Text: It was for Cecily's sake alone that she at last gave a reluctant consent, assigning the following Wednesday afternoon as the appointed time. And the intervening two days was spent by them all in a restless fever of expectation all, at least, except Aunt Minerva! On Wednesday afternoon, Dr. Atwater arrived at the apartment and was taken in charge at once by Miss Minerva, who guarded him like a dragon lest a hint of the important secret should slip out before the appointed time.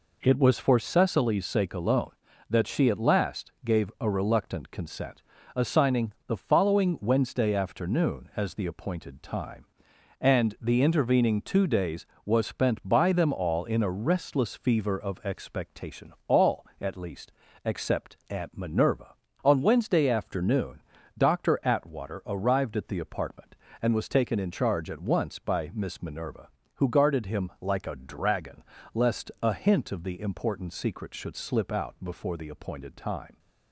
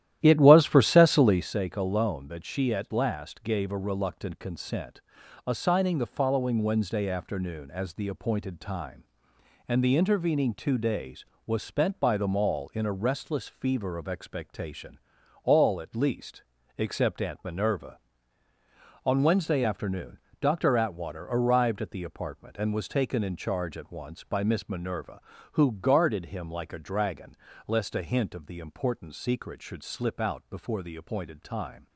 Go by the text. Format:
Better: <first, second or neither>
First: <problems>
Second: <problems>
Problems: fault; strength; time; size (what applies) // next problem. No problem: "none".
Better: first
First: pauses between "dragon" and "lest"; slight; at 28.6 s; 0.32 s long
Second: starts louder than the rest; strong; until 1.6 s; 12.5 dB // pauses between "expectation" and "all"; at 14.9 s; 0.44 s long // pauses between "dragon" and "lest"; slight; at 27.3 s; 0.32 s long